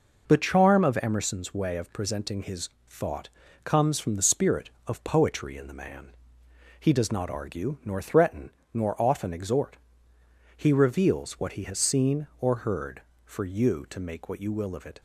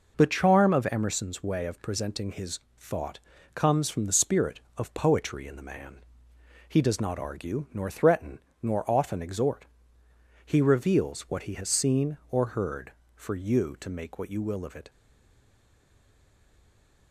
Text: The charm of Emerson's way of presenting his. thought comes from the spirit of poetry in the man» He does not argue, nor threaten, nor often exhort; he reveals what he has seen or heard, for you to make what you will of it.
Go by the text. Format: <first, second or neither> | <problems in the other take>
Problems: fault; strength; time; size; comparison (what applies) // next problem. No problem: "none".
first | pauses between "thought" and "comes"; at 3.1 s; 0.38 s long; also in the first // pauses between "man" and "He"; noticeable; at 6.0 s; 0.66 s long; noticeable in the first // stays silent after the last word; from 14.8 s on; 2.3 s long